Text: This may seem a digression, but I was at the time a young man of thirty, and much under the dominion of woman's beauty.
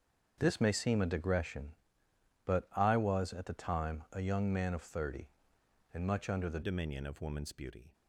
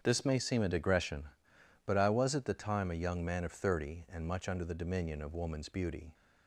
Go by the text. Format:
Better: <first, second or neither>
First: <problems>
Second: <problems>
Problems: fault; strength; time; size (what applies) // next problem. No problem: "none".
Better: second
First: starts louder than the rest; until 1.3 s; 7 dB // changes voice at "dominion"; from 6.6 s on; 1.3 s long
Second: starts louder than the rest; strong; until 1.0 s; 8 dB